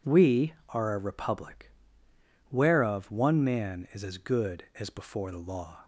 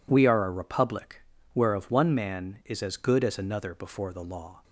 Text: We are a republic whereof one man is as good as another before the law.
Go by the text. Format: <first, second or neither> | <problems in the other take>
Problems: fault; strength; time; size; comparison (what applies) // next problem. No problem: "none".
second | pauses between "republic" and "whereof"; noticeable; at 1.7 s; 0.80 s long; slight in the second // skips "another"; at 4.8 s